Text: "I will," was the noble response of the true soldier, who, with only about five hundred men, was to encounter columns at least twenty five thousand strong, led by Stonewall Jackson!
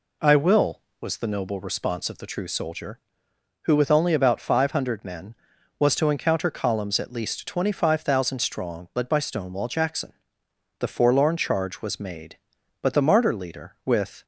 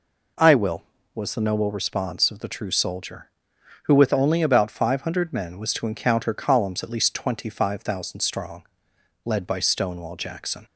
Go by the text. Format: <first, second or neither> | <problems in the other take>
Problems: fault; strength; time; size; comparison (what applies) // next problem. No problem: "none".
second | goes on to say "The forlorn charge was made but the martyr leader with"; strong; from 10.7 s on; 3.4 s long